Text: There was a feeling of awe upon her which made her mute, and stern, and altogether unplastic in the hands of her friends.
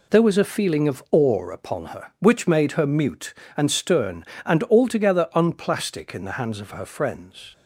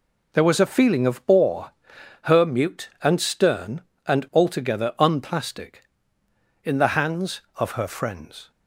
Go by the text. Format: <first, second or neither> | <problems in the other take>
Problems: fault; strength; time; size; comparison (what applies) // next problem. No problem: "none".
first | skips "upon her which made"; at 1.9 s